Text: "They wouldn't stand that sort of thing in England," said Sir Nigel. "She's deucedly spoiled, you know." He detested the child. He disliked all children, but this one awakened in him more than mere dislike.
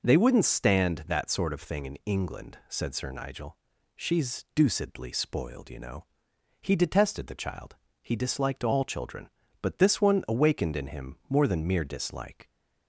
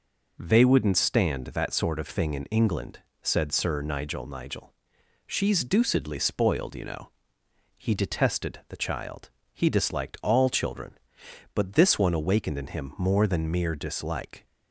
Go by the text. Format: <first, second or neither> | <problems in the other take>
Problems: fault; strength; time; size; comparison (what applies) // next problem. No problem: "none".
first | says "Nigel" twice; at 4.2 s